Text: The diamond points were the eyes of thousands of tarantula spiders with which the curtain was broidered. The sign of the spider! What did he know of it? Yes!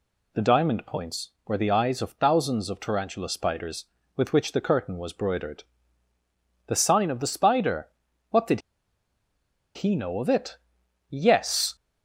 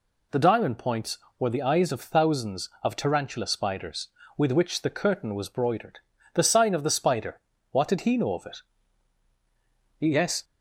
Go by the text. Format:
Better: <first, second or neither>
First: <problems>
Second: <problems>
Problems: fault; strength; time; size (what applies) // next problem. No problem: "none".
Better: second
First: pauses between "did" and "he"; at 8.6 s; 1.1 s long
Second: none